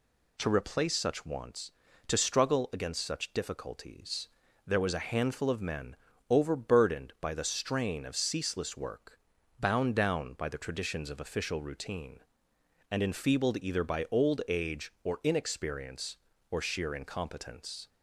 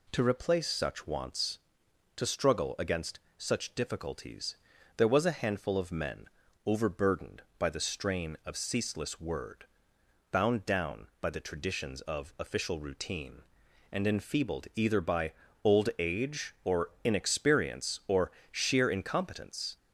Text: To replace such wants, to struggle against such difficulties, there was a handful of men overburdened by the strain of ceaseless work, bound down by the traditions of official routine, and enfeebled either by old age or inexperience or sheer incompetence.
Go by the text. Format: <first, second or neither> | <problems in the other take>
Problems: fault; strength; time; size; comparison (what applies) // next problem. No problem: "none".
first | pauses between "against" and "such"; slight; at 3.1 s; 0.18 s long // pauses between "men" and "overburdened"; slight; at 6.2 s; 0.36 s long; slight in the first // says "word" for "work"; at 9.2 s // pauses between "by" and "old"; slight; at 15.3 s; 0.30 s long // pauses between "or" and "sheer"; slight; at 18.3 s; 0.20 s long